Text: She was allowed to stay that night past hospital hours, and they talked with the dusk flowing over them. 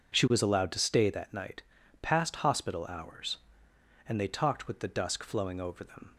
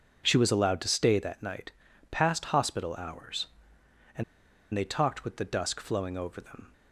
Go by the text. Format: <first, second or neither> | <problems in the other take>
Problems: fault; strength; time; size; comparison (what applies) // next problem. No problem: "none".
first | pauses between "night" and "past"; at 1.7 s; 0.40 s long; also in the first // pauses between "and" and "they"; noticeable; at 4.2 s; 0.50 s long